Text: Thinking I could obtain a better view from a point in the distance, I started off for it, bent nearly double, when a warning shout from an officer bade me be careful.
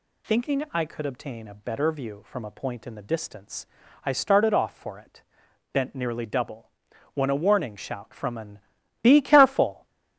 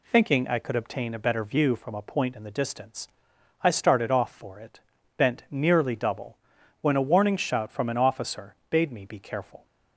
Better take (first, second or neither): second